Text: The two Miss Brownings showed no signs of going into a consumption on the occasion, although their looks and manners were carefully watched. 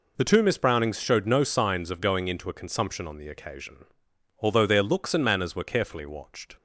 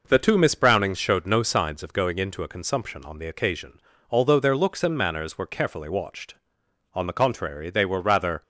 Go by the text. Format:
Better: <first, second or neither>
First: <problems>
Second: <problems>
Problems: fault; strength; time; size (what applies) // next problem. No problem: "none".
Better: first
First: none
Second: goes on to say "On the contrary they were rather"; from 6.9 s on; 1.4 s long